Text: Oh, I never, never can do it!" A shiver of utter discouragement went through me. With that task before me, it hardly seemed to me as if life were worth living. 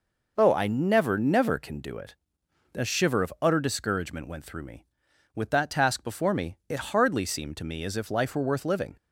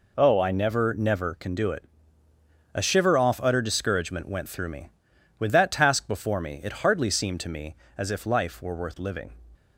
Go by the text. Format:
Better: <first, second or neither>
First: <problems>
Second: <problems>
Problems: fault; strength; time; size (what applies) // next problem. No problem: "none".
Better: first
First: none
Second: says "off" for "of"; at 3.1 s